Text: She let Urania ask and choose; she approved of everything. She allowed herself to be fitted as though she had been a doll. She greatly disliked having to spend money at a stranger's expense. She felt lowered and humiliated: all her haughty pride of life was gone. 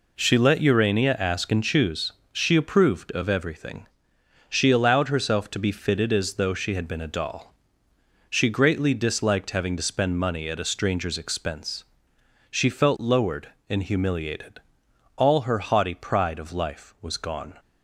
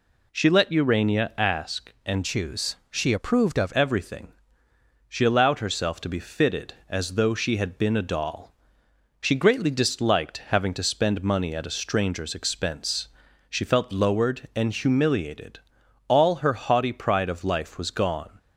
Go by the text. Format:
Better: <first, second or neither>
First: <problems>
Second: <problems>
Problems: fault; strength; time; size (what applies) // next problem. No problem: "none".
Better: first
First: none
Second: changes voice from "choose" to "of"; from 2.2 to 3.7 s; 1.5 s long